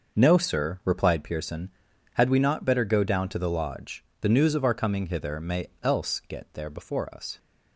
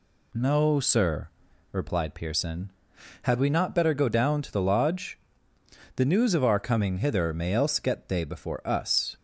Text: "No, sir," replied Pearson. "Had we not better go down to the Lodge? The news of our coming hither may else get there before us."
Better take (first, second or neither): first